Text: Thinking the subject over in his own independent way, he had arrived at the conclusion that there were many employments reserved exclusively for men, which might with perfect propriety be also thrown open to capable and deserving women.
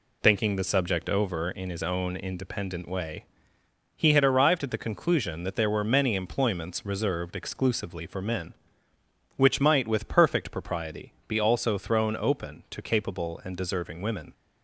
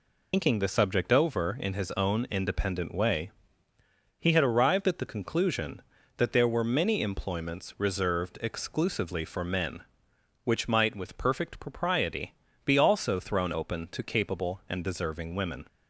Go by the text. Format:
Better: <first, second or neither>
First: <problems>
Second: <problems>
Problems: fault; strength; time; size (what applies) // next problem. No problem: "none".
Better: first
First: pauses between "propriety" and "be"; slight; at 11.1 s; 0.16 s long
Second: loses the start of "Thinking"; at 0.3 s; 95 ms // pauses between "propriety" and "be"; slight; at 12.3 s; 0.32 s long